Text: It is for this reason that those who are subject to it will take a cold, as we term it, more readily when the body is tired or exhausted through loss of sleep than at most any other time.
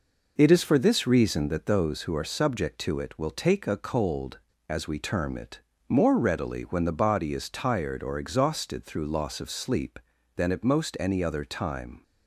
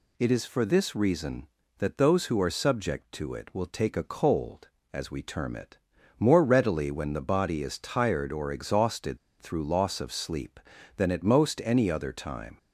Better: first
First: none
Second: pauses between "exhausted" and "through"; slight; at 9.1 s; 0.22 s long

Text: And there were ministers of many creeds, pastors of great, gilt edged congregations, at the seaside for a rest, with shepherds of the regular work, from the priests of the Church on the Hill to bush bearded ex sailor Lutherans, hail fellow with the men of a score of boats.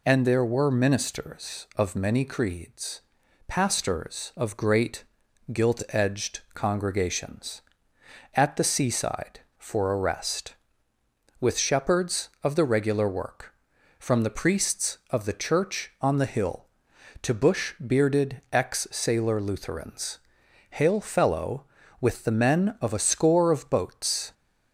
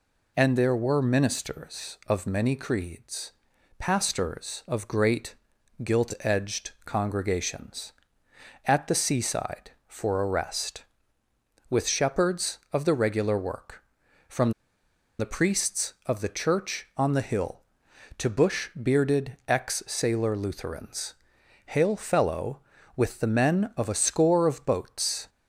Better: first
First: none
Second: pauses between "from" and "the"; noticeable; at 14.5 s; 0.68 s long

